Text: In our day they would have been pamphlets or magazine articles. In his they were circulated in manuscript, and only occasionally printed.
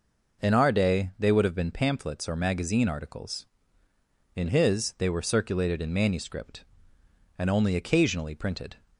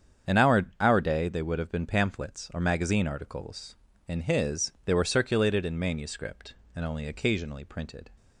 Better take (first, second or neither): first